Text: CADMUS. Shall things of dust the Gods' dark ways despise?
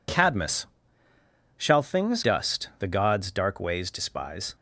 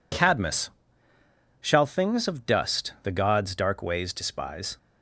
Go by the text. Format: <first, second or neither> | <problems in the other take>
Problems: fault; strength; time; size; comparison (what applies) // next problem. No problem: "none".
second | skips "of"; at 2.2 s